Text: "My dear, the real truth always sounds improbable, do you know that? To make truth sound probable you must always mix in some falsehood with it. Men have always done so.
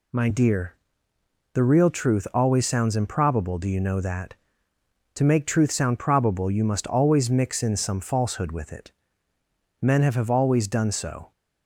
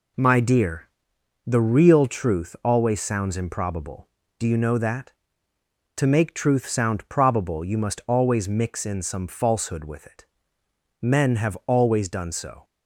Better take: second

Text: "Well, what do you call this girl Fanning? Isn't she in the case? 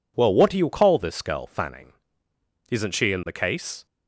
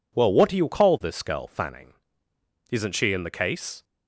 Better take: neither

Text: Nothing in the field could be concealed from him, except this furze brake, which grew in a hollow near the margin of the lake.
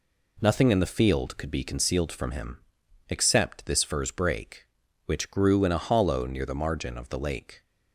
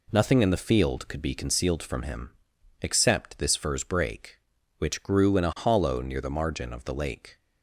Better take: neither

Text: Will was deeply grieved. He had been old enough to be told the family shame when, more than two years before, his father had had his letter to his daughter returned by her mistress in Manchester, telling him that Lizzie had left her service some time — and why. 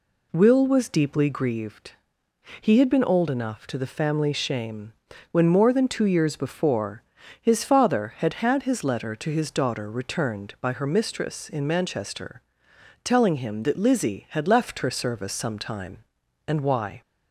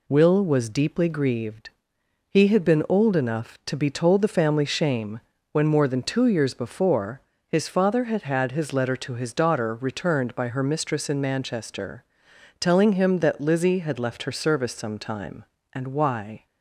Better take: second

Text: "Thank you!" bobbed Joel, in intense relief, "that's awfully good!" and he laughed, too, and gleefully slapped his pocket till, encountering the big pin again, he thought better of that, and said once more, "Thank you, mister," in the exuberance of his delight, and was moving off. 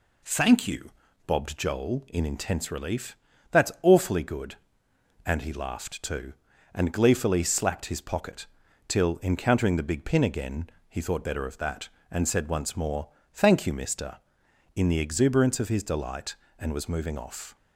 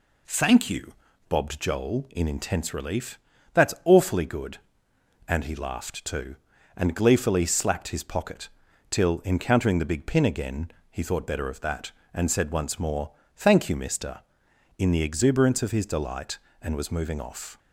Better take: neither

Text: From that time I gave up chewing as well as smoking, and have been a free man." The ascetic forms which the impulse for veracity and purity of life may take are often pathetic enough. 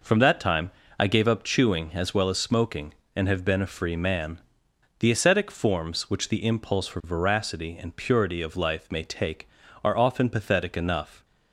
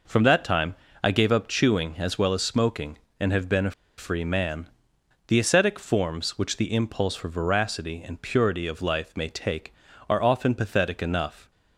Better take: first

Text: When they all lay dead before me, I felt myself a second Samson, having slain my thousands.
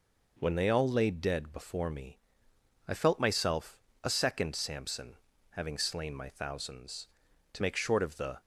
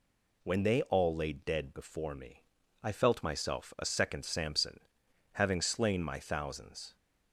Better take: second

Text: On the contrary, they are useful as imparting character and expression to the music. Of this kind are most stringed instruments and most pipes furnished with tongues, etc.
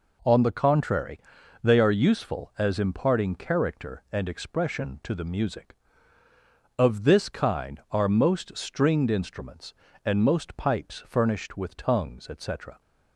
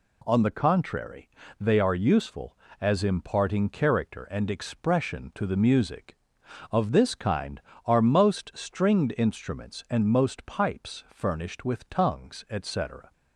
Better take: neither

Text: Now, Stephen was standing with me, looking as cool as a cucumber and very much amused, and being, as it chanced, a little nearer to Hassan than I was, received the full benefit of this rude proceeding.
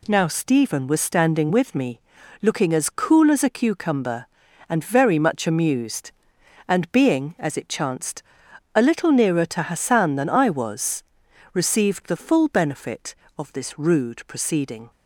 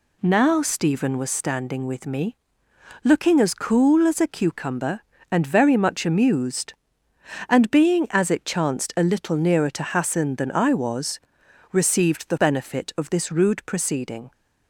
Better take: first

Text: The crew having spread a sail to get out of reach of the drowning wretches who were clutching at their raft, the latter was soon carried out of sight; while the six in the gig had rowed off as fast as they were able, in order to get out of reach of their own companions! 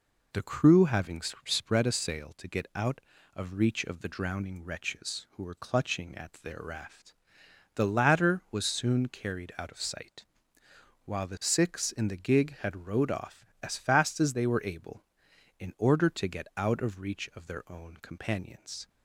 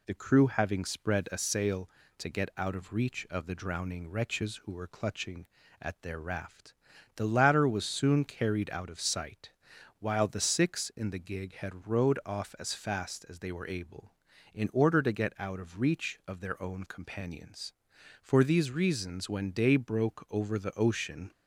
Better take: first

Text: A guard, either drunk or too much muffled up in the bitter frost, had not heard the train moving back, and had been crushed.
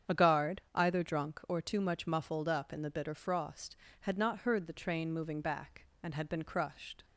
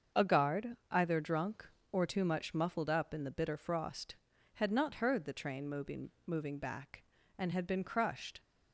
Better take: first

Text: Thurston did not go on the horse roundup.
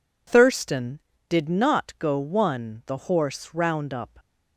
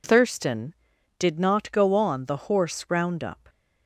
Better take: second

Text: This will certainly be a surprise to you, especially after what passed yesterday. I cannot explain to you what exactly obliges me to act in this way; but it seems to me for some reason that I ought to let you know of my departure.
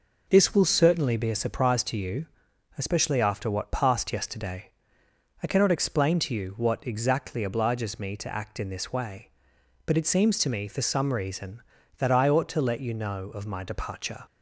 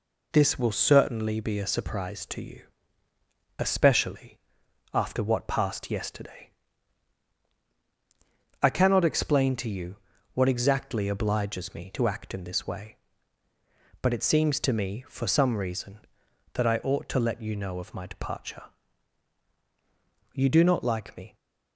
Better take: first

